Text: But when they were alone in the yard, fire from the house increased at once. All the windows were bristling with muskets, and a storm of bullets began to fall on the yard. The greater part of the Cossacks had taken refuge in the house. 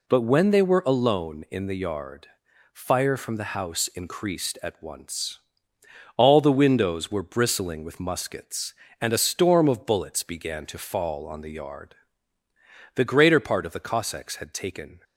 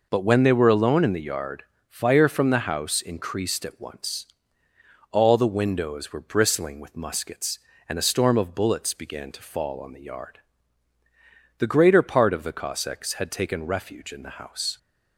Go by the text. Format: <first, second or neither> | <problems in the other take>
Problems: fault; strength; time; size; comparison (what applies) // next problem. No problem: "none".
second | stops before "refuge in the house"; at 15.0 s